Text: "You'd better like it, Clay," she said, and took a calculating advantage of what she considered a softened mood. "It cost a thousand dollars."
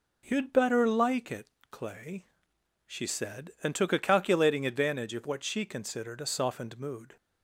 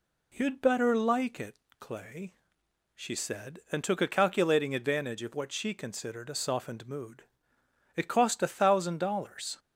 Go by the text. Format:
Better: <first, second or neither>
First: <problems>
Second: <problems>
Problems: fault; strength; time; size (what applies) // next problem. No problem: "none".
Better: second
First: stops before "It cost a thousand dollars"; at 7.1 s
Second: none